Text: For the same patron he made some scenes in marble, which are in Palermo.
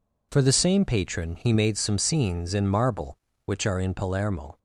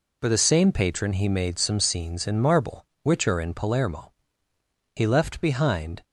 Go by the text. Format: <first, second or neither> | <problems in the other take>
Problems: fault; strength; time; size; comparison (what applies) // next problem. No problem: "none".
first | goes on to say "He left behind"; noticeable; from 4.9 s on; 1.1 s long